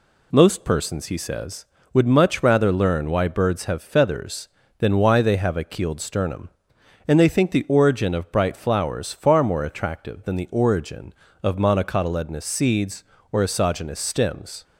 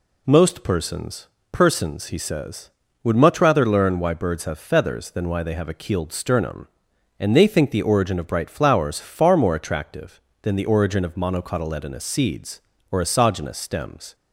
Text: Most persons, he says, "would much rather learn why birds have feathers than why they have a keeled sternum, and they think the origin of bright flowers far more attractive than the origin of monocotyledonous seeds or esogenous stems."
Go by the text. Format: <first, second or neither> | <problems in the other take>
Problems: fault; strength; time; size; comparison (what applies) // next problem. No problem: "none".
first | says "persons" twice; at 1.5 s